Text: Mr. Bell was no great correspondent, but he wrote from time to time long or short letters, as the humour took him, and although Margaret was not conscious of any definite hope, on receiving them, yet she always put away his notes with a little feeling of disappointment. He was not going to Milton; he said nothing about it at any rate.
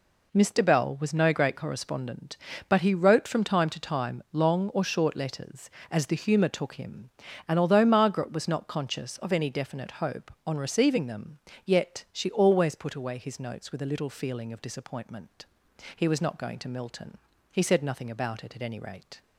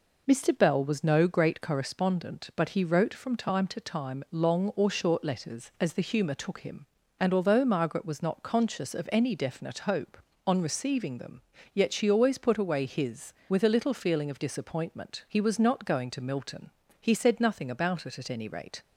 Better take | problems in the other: first | skips "notes"; at 13.4 s

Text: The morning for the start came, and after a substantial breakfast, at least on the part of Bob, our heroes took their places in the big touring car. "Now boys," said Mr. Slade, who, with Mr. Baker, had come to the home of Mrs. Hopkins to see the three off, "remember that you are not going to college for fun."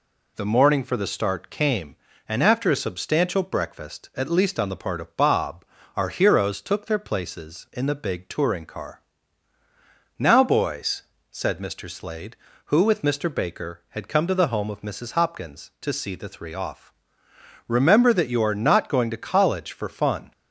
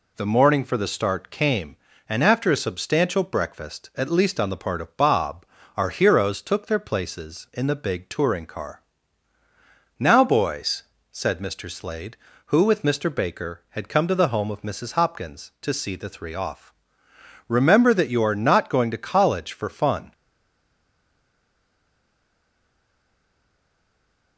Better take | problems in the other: first | stays silent after the last word; strong; from 20.1 s on; 4.2 s long

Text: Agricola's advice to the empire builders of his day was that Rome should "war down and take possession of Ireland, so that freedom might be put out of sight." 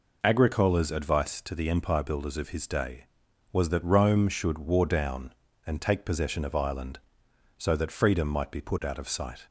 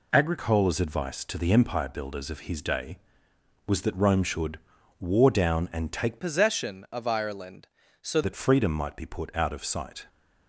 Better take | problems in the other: first | pauses between "should" and "war"; at 4.5 s; 0.44 s long // changes voice from "possession" to "so"; from 6.2 to 8.2 s; 2.0 s long

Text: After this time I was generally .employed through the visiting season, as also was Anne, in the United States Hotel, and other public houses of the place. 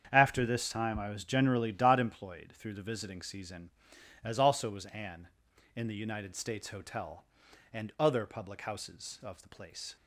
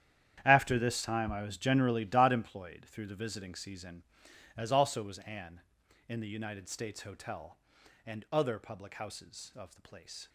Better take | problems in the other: first | gets quieter; strong; throughout; 14.5 dB // starts louder than the rest; strong; until 1.4 s; 10 dB; strong in the first

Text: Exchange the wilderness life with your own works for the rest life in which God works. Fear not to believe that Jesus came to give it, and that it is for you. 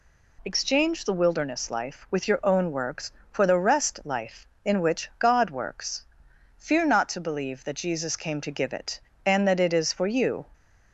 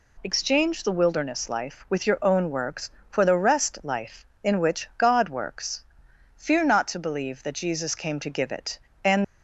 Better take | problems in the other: first | stops before "that it is for you"; at 9.2 s

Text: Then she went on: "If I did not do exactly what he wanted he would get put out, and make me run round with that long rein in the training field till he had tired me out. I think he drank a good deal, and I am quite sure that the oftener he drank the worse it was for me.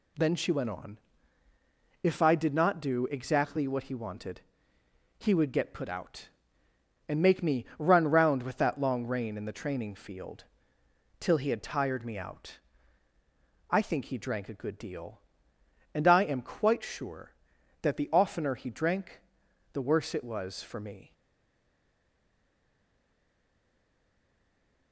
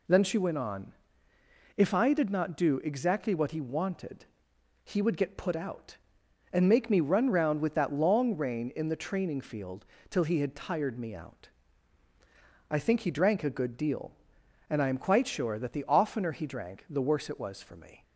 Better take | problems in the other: second | pauses between "wanted" and "he"; noticeable; at 4.4 s; 0.78 s long; noticeable in the second // pauses between "field" and "till"; noticeable; at 10.4 s; 0.78 s long; slight in the second // pauses between "drank" and "the"; noticeable; at 19.2 s; 0.52 s long // stays silent after the last word; strong; from 21.1 s on; 3.8 s long

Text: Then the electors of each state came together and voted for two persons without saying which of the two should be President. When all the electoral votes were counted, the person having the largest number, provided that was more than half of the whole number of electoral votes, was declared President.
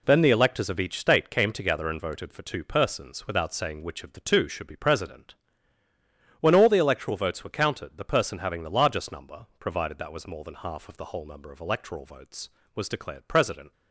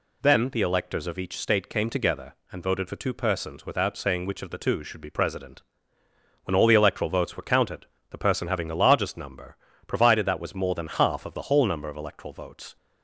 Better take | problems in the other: first | stops before "was declared President"; at 12.7 s

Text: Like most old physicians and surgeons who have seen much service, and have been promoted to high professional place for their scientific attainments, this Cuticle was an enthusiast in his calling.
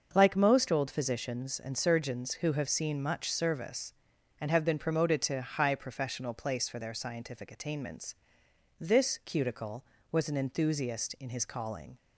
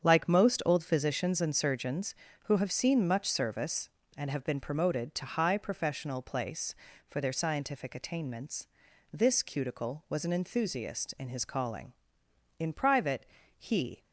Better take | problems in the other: first | starts louder than the rest; strong; until 1.0 s; 7.5 dB; also in the first // goes on to say "In private he"; from 12.5 s on; 1.4 s long

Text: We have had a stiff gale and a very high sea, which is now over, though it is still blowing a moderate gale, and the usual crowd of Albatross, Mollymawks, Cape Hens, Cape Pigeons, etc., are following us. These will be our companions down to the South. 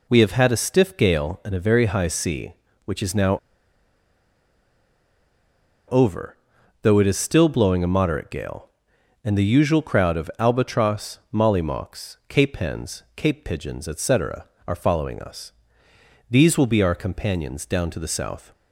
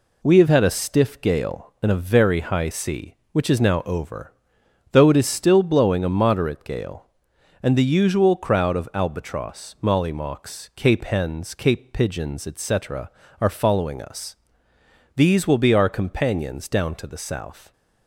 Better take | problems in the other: second | pauses between "now" and "over"; strong; at 3.3 s; 2.5 s long

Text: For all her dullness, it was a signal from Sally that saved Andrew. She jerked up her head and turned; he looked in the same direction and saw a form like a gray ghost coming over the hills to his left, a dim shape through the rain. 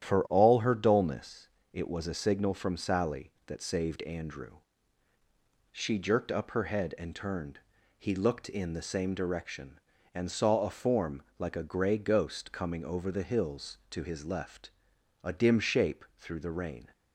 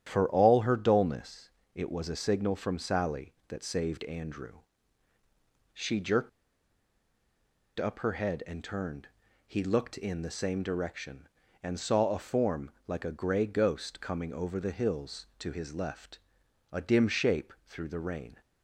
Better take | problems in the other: first | starts louder than the rest; strong; until 1.0 s; 10.5 dB; strong in the first // pauses between "jerked" and "up"; strong; at 6.2 s; 1.4 s long // pauses between "form" and "like"; slight; at 12.7 s; 0.16 s long; slight in the first

